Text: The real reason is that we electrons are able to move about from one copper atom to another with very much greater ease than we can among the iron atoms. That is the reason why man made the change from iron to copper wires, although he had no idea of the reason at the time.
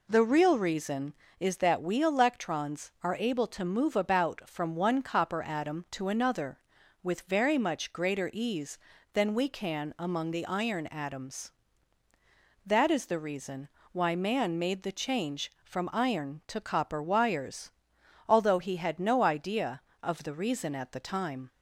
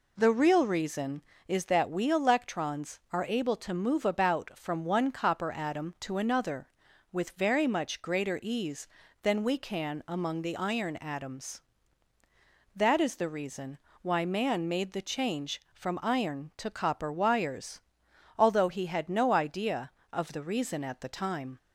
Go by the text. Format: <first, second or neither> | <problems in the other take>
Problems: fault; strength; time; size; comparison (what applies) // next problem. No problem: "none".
neither | pauses between "reason" and "why"; slight; the same in both